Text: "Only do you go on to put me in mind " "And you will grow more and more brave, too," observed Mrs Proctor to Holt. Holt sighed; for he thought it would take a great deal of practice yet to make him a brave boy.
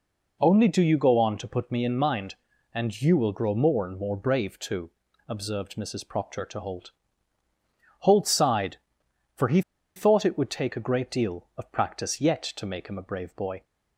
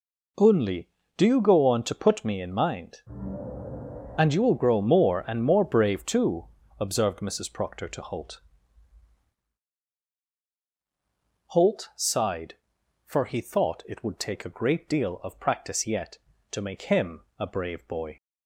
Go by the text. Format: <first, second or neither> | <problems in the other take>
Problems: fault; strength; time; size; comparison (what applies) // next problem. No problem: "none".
second | pauses between "he" and "thought"; slight; at 9.6 s; 0.35 s long